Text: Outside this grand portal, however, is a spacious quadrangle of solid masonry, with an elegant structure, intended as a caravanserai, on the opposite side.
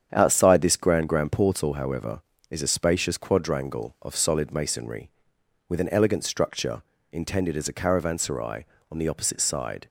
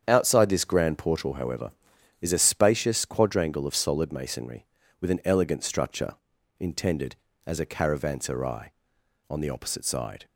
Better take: second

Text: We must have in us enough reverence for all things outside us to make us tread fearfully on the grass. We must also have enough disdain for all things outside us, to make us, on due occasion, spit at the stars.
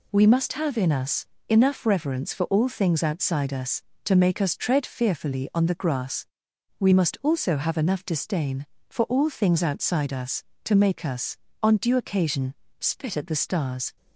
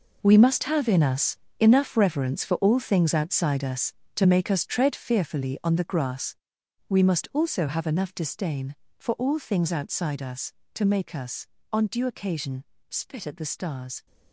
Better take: first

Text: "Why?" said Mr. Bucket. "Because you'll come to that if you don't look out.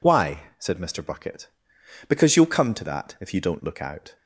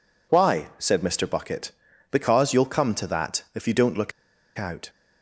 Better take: first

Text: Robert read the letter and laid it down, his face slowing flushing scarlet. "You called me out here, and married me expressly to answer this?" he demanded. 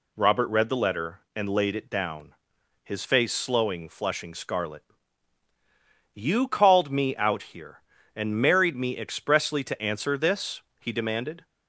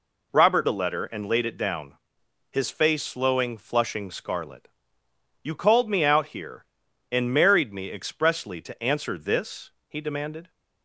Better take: first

